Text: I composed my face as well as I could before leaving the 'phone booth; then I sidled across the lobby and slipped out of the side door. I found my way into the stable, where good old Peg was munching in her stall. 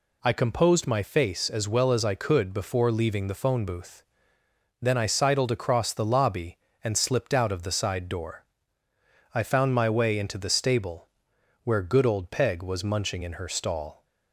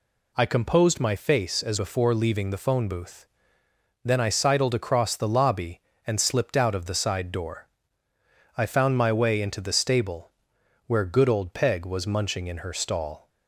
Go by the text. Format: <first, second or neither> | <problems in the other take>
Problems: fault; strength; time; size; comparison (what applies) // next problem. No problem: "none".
first | skips "well as I could"; at 1.7 s